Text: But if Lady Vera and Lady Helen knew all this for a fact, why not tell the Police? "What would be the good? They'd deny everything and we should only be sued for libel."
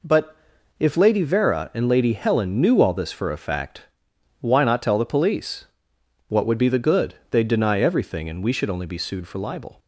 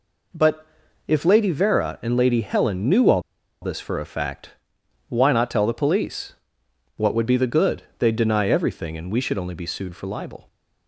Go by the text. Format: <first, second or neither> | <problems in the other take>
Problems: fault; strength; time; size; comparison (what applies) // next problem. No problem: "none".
first | pauses between "But" and "if"; at 0.6 s; 0.42 s long; also in the first // pauses between "all" and "this"; at 3.2 s; 0.41 s long